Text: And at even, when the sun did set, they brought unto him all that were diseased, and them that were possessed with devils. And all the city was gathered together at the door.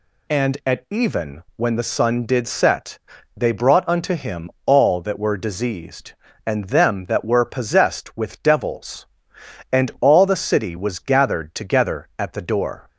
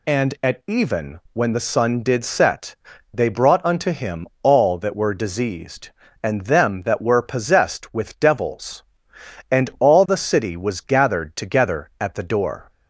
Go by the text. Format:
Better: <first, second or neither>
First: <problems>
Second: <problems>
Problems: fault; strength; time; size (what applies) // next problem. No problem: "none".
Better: neither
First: none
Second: none